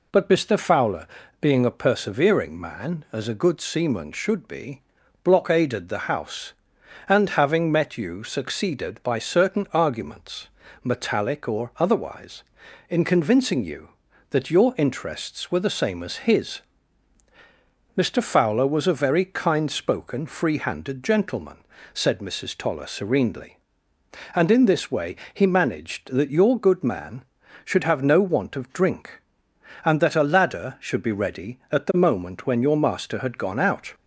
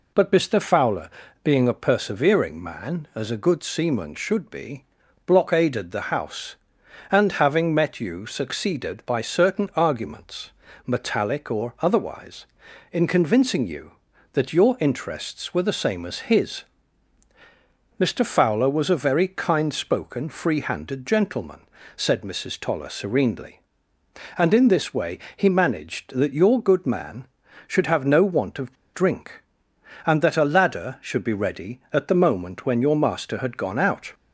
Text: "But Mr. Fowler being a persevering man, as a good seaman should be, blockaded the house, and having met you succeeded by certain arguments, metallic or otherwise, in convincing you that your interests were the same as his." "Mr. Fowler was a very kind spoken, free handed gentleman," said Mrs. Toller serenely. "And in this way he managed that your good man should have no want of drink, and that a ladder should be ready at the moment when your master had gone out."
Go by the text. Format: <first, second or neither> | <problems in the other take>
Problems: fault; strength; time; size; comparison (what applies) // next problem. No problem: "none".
first | pauses between "Fowler" and "being"; slight; at 1.0 s; 0.34 s long; slight in the first // pauses between "way" and "he"; slight; at 25.1 s; 0.18 s long; slight in the first // pauses between "of" and "drink"; slight; at 28.7 s; 0.19 s long